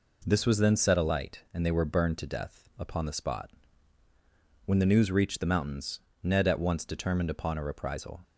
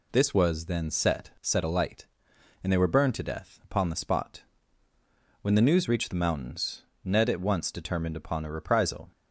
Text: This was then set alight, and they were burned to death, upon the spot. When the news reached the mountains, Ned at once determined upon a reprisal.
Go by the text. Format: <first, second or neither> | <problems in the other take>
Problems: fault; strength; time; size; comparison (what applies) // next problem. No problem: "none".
first | says "set" twice; at 1.4 s